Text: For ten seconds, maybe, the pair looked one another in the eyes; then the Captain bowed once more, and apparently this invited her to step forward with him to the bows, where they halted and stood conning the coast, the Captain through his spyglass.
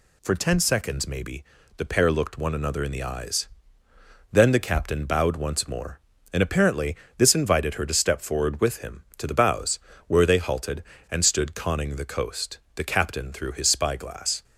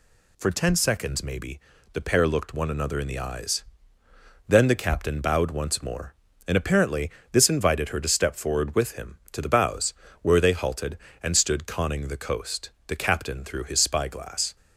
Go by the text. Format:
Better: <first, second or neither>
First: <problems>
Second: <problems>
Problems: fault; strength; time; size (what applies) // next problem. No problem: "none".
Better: neither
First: pauses between "apparently" and "this"; slight; at 6.9 s; 0.20 s long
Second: pauses between "apparently" and "this"; slight; at 7.1 s; 0.20 s long